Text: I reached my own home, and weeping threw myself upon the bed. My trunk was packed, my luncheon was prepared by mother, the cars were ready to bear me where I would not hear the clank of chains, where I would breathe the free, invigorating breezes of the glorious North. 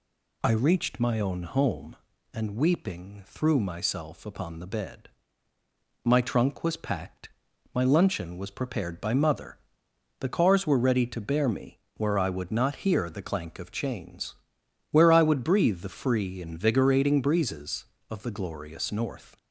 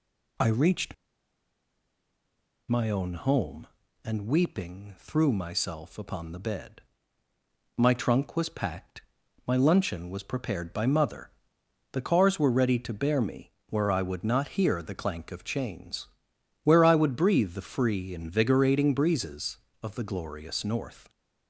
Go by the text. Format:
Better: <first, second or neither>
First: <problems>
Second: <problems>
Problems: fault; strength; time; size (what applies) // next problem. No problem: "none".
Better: first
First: pauses between "me" and "where"; slight; at 11.7 s; 0.18 s long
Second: pauses between "reached" and "my"; strong; at 0.9 s; 1.7 s long // pauses between "me" and "where"; slight; at 13.5 s; 0.18 s long